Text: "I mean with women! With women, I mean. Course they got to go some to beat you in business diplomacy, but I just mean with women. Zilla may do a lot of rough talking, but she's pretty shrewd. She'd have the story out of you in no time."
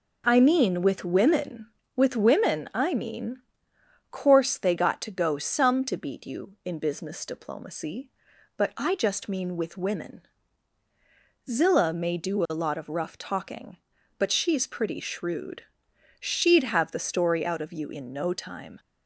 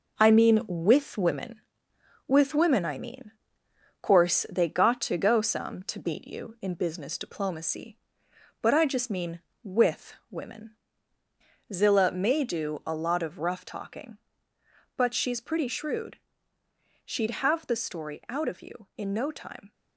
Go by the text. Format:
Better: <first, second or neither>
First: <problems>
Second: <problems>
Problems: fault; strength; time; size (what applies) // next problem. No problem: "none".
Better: first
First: none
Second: gets quieter; noticeable; throughout; 5.5 dB // pauses between "with" and "women"; slight; at 10.1 s; 0.16 s long